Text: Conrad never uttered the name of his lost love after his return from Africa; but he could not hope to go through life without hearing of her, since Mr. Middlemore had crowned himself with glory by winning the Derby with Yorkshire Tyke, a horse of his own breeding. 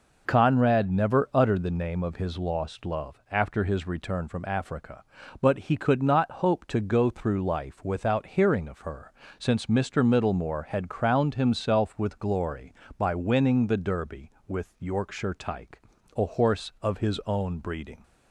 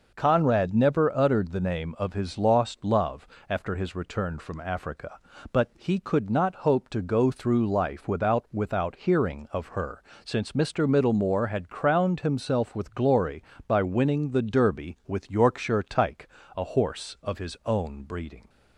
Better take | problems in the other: first | pauses between "love" and "after"; slight; at 3.2 s; 0.22 s long // says "without" twice; at 8.5 s

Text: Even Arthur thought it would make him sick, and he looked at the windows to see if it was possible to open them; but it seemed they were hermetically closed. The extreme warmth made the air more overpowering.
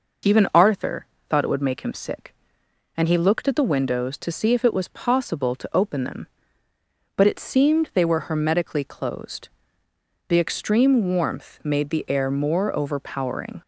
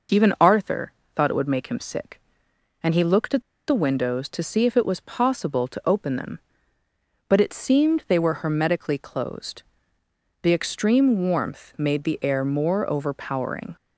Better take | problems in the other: first | pauses between "Arthur" and "thought"; slight; at 0.9 s; 0.24 s long; slight in the first // pauses between "at" and "the"; slight; at 3.4 s; 0.25 s long

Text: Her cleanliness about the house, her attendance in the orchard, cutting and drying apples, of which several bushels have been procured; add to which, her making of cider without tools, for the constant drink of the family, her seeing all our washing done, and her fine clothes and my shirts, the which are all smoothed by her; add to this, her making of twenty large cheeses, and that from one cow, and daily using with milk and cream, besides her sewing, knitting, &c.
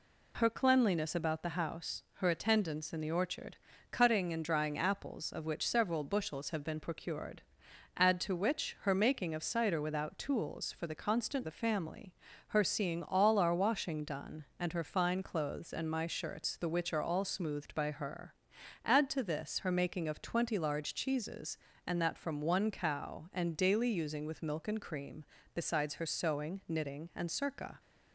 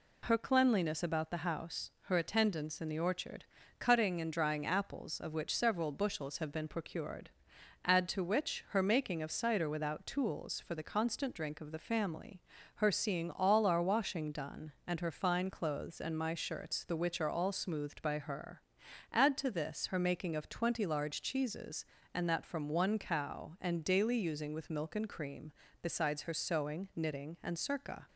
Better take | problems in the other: second | skips "drink of"; at 11.4 s

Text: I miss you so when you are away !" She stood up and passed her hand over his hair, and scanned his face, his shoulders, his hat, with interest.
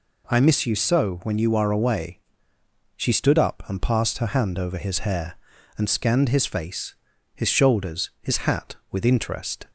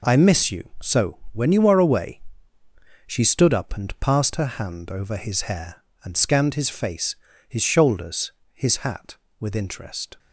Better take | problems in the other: first | gets quieter; noticeable; throughout; 5.5 dB

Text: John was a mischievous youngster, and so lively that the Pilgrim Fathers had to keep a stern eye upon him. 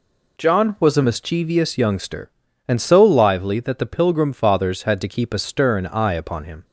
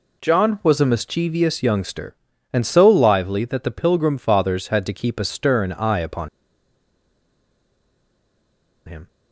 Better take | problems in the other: first | pauses between "upon" and "him"; strong; at 6.2 s; 2.5 s long

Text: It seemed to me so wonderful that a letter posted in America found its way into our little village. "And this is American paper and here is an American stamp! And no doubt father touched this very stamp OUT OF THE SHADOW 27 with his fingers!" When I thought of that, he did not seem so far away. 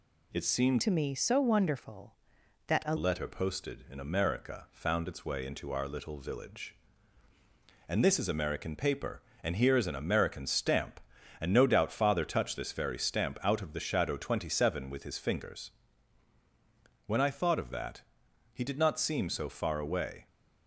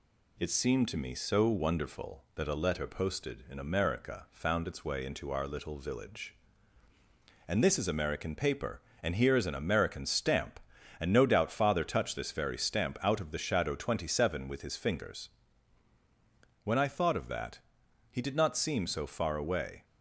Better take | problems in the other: second | changes voice from "to" to "a"; from 0.8 to 2.9 s; 2.1 s long

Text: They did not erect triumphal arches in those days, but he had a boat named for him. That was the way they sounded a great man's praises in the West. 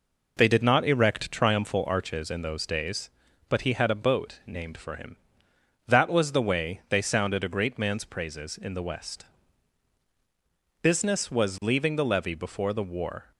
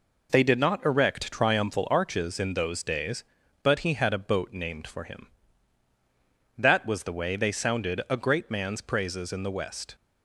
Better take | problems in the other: second | goes on to say "Business was leaving the levee before the war"; strong; from 10.8 s on; 2.4 s long

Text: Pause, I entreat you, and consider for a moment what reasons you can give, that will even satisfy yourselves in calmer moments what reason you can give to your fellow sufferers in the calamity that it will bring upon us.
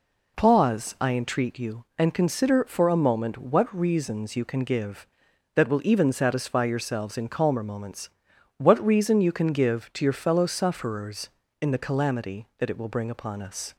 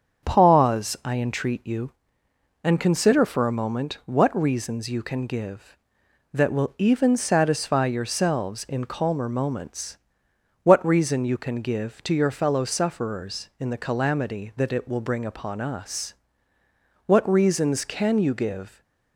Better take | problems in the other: first | starts louder than the rest; until 1.3 s; 7 dB // pauses between "moments" and "what"; noticeable; at 9.9 s; 0.66 s long; noticeable in the first // goes on to say "What reasons can you give"; strong; from 17.0 s on; 1.7 s long

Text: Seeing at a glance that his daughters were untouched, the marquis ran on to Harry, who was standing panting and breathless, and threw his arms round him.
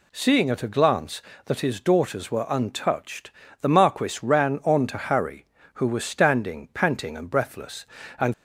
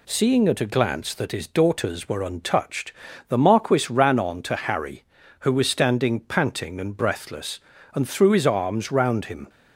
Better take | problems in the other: second | stops before "threw his arms round him"; at 8.3 s

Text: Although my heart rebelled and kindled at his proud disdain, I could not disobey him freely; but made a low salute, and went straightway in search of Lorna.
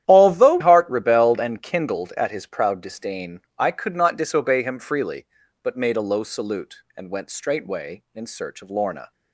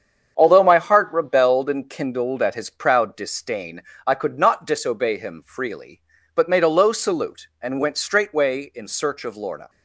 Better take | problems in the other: second | starts louder than the rest; strong; until 1.0 s; 11.5 dB; strong in the second // skips "my"; at 0.5 s

